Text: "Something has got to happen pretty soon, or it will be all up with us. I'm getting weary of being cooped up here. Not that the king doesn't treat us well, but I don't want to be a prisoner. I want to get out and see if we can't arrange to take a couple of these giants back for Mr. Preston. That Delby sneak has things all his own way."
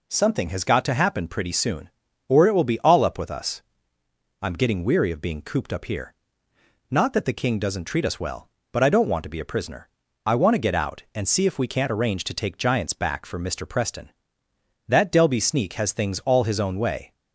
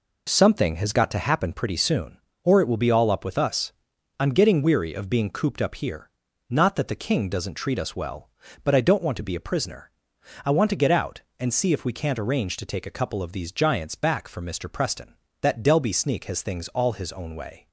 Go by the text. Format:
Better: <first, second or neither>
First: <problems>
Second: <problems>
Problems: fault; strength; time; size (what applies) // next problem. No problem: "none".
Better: second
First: skips "a couple of these"; at 12.5 s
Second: none